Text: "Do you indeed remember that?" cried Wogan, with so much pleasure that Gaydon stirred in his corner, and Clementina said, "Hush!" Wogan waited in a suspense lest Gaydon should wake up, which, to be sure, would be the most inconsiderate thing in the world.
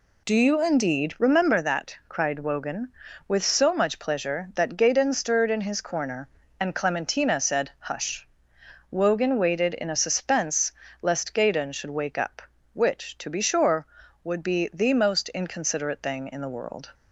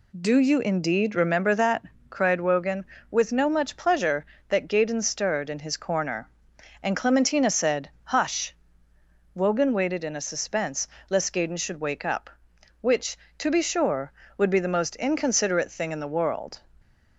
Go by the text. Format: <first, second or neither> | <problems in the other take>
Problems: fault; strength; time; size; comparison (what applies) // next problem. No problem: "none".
first | says "no" for "so"; at 3.2 s // pauses between "suspense" and "lest"; slight; at 10.8 s; 0.22 s long; slight in the first